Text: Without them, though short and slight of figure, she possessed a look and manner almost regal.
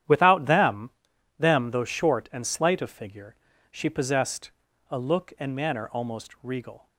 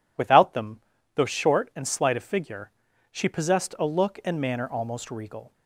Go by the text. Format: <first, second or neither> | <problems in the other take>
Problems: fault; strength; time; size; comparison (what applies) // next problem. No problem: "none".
second | starts louder than the rest; strong; until 1.5 s; 10.5 dB // says "them" twice; at 1.3 s // pauses between "possessed" and "a"; at 4.5 s; 0.38 s long